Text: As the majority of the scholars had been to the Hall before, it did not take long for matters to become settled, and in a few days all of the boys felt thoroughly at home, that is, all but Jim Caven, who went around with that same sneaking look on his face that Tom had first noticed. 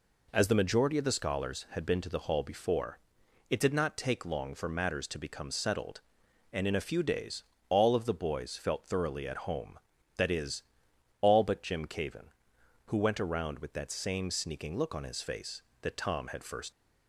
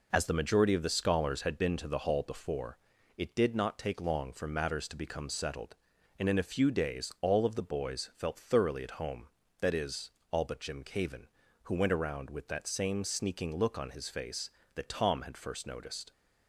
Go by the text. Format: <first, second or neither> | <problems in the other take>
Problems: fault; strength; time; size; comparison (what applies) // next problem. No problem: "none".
second | pauses between "days" and "all"; slight; at 7.4 s; 0.24 s long // stops before "noticed"; at 16.7 s